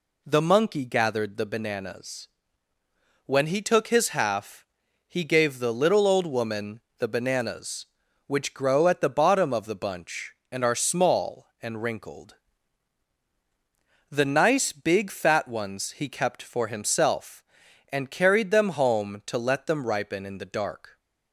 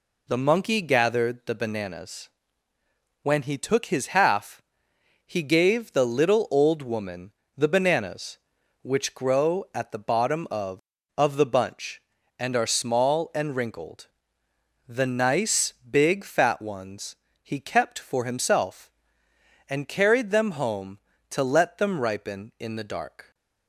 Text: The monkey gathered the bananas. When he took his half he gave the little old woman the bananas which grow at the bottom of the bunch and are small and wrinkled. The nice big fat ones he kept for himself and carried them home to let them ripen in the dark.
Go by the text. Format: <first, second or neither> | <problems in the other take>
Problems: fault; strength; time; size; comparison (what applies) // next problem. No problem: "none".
first | pauses between "half" and "he"; noticeable; at 4.5 s; 0.66 s long; also in the first // pauses between "woman" and "the"; slight; at 7.3 s; 0.24 s long; slight in the first // says "of" twice; at 11.1 s // pauses between "nice" and "big"; slight; at 15.7 s; 0.18 s long // pauses between "ones" and "he"; slight; at 17.1 s; 0.26 s long